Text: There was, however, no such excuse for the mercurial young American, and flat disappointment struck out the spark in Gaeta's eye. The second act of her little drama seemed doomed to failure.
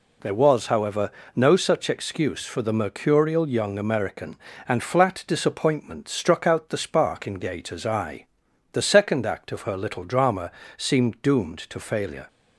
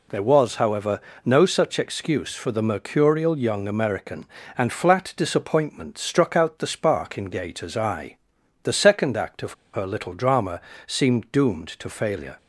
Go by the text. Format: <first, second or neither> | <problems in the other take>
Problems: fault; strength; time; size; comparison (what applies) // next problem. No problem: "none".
first | pauses between "of" and "her"; slight; at 9.5 s; 0.21 s long // pauses between "drama" and "seemed"; slight; at 10.6 s; 0.26 s long; slight in the first